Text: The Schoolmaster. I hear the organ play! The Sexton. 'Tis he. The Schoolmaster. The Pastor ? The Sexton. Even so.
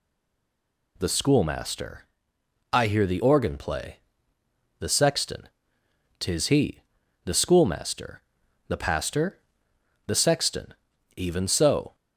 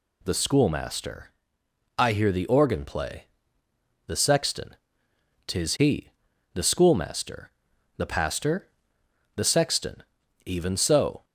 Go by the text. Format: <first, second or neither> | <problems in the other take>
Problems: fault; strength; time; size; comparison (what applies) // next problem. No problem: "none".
second | stays silent before the first word; slight; until 0.9 s; 0.9 s long